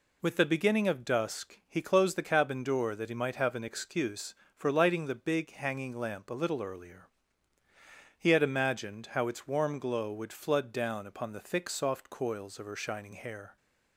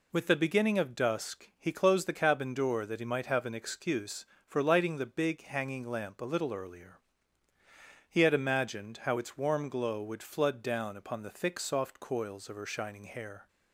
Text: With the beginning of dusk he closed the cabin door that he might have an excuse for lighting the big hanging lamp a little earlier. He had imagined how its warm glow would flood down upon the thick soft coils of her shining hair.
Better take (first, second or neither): neither